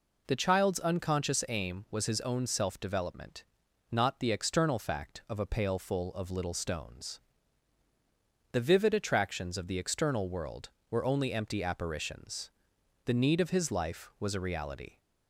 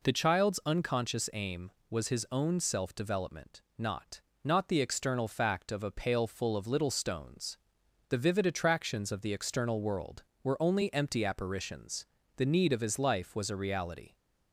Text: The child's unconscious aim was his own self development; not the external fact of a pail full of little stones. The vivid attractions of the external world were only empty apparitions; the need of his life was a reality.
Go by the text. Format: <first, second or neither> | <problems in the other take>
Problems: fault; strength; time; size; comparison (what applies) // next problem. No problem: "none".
first | says "not" twice; at 4.4 s